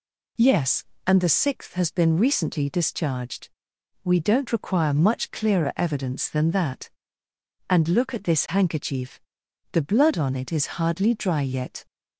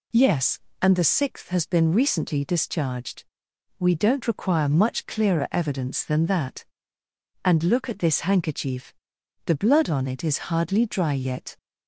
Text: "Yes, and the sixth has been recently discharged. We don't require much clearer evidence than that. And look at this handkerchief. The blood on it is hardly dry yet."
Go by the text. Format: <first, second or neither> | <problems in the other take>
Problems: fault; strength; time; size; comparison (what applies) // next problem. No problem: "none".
neither | none